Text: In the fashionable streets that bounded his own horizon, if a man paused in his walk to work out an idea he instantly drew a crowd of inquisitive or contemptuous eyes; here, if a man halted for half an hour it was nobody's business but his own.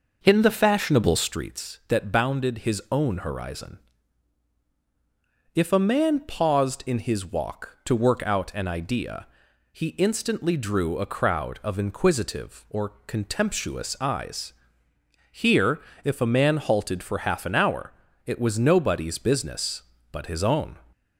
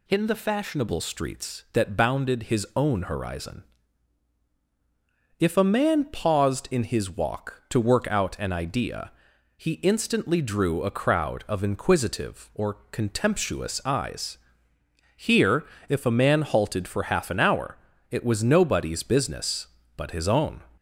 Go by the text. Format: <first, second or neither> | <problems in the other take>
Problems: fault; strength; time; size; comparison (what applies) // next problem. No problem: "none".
second | starts louder than the rest; noticeable; until 1.4 s; 5.5 dB // pauses between "idea" and "he"; noticeable; at 9.2 s; 0.46 s long; noticeable in the second // pauses between "or" and "contemptuous"; slight; at 12.8 s; 0.18 s long; slight in the second // pauses between "hour" and "it"; slight; at 17.9 s; 0.36 s long; slight in the second